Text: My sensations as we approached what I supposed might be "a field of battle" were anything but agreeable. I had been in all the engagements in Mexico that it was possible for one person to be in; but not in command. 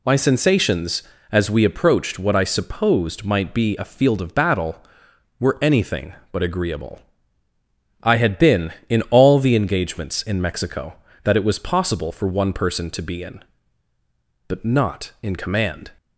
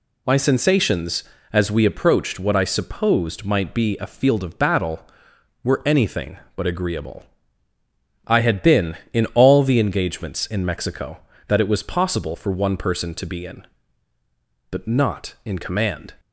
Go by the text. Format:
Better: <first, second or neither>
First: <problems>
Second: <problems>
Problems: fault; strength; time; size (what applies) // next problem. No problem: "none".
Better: neither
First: none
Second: none